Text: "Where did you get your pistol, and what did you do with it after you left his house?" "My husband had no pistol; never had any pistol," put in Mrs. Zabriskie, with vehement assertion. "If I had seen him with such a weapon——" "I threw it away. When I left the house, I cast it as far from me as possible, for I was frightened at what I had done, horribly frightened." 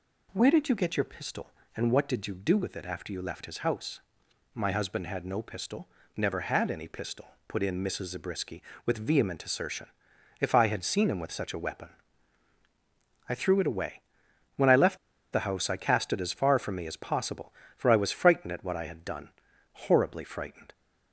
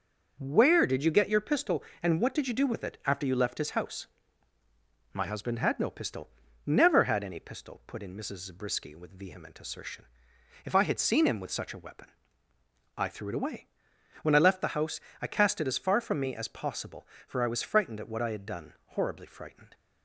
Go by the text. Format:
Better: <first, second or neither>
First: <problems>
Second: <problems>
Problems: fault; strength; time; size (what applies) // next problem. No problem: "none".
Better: second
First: pauses between "left" and "the"; at 14.9 s; 0.36 s long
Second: none